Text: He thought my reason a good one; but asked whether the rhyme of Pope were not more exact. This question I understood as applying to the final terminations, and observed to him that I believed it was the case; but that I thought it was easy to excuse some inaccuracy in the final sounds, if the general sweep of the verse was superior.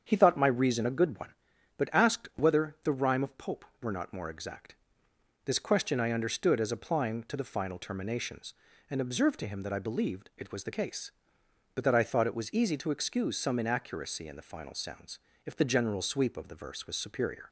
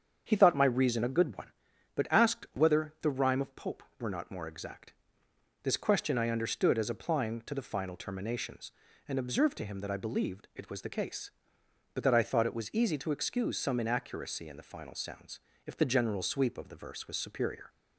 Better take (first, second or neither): neither